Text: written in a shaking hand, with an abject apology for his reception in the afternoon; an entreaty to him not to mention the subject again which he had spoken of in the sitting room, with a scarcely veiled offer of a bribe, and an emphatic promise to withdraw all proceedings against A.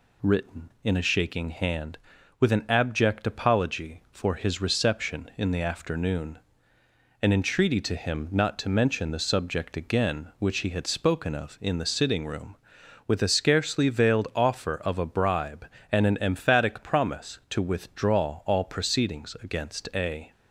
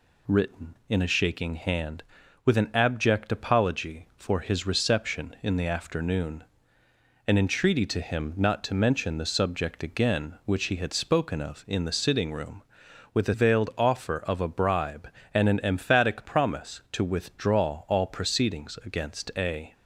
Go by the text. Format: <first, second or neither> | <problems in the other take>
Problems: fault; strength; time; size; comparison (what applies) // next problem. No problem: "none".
first | skips "scarcely"; at 13.3 s